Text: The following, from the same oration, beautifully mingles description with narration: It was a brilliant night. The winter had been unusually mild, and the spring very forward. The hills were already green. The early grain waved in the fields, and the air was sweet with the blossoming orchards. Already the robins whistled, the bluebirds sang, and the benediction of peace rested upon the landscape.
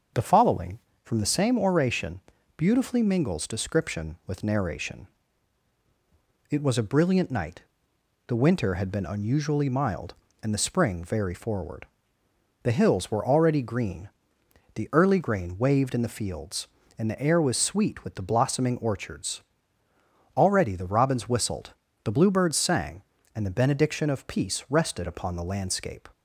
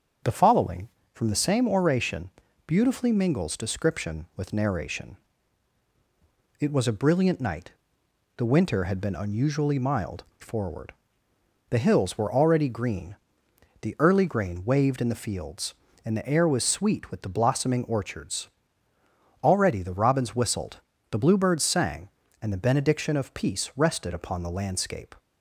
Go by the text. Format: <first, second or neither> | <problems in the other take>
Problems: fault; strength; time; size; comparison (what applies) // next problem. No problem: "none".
first | starts louder than the rest; until 1.5 s; 7 dB; also in the first // skips "and the spring very"; at 10.3 s